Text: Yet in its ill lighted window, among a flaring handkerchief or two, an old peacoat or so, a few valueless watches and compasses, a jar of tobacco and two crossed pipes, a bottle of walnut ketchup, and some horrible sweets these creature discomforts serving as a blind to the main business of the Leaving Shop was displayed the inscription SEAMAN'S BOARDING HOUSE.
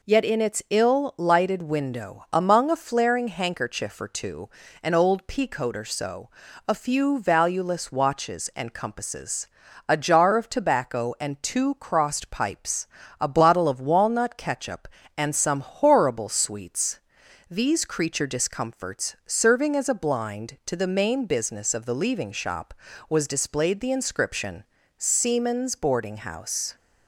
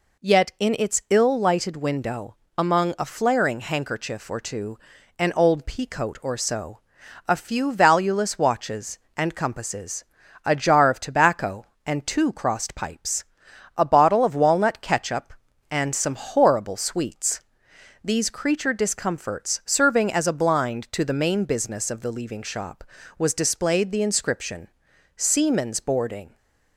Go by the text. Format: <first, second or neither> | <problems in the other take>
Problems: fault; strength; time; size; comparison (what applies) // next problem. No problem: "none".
first | pauses between "sweets" and "these"; noticeable; at 17.4 s; 0.64 s long; noticeable in the first // pauses between "inscription" and "SEAMAN'S"; noticeable; at 24.6 s; 0.48 s long; slight in the first // stops before "HOUSE"; at 26.3 s